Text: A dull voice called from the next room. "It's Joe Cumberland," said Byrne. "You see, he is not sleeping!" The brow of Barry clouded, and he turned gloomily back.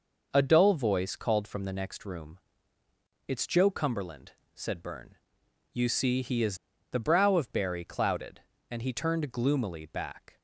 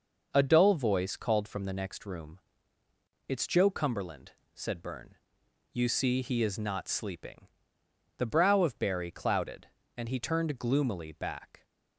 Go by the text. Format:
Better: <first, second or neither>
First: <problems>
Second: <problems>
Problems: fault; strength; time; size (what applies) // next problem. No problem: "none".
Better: second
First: skips "not sleeping"; at 6.7 s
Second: none